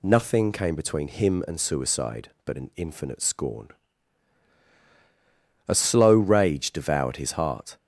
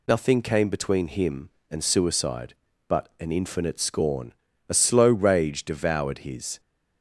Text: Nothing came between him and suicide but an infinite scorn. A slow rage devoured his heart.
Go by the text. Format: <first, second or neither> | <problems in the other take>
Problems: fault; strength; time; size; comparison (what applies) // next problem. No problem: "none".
first | stops before "heart"; at 6.5 s